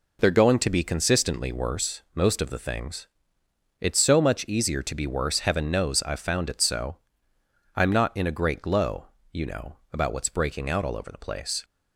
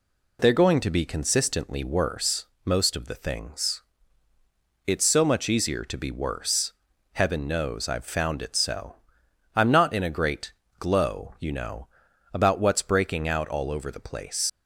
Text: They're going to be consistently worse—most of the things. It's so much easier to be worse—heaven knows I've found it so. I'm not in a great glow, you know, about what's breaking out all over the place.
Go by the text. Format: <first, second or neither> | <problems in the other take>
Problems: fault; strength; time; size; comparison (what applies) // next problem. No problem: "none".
first | pauses between "great" and "glow"; slight; at 10.5 s; 0.26 s long // leaves "place" unfinished; at 14.4 s; 65 ms